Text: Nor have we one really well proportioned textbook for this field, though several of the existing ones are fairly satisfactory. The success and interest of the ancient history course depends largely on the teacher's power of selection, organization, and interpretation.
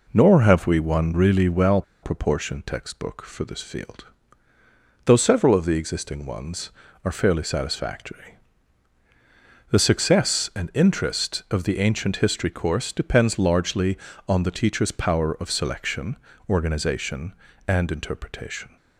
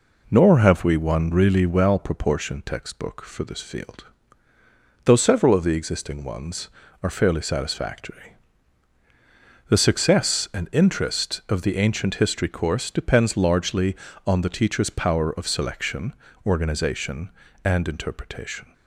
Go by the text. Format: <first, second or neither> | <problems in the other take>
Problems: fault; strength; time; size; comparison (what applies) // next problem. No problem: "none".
second | pauses between "well" and "proportioned"; slight; at 1.8 s; 0.20 s long